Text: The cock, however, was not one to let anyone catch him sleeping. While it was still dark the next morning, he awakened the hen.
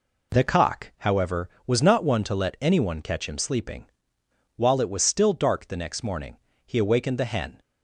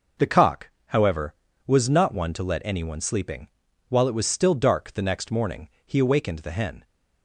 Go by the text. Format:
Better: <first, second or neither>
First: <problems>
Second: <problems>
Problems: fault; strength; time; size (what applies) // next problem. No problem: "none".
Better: first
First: none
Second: skips "catch him"; at 3.0 s